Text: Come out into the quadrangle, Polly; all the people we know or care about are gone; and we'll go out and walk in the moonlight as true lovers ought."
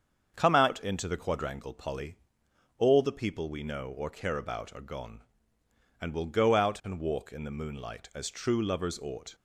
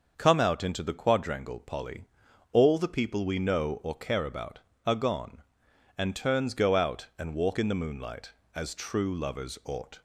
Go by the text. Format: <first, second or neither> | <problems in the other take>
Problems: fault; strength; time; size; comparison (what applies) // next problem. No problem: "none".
first | starts louder than the rest; until 1.1 s; 6.5 dB; also in the first // says "turns" for "we'll"; at 6.1 s